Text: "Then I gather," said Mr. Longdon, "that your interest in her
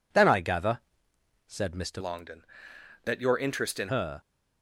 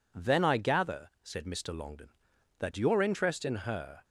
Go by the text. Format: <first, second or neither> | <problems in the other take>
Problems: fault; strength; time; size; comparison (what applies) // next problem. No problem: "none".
second | changes voice from "Longdon" to "in"; from 1.9 to 3.8 s; 1.9 s long